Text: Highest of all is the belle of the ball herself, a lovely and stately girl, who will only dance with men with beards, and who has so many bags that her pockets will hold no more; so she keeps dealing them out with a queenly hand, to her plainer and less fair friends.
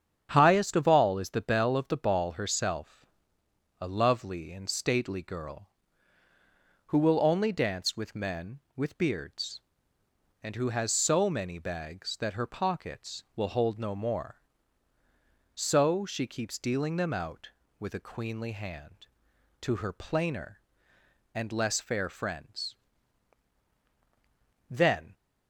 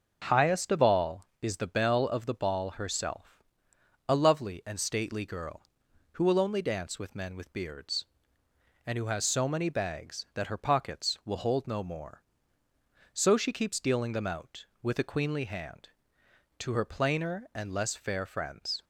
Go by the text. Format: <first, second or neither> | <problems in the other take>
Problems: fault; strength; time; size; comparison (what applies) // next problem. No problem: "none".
second | starts louder than the rest; strong; until 1.3 s; 8.5 dB; noticeable in the second // goes on to say "Then"; slight; from 24.7 s on; 0.42 s long